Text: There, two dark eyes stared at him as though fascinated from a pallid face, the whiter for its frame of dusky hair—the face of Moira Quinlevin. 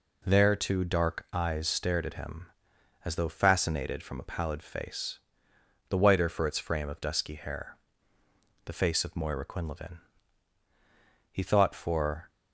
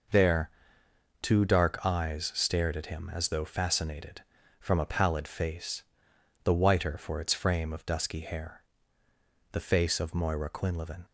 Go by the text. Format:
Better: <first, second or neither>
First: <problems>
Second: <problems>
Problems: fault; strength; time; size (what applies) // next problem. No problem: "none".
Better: second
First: goes on to say "He thought for"; noticeable; from 11.3 s on; 0.98 s long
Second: none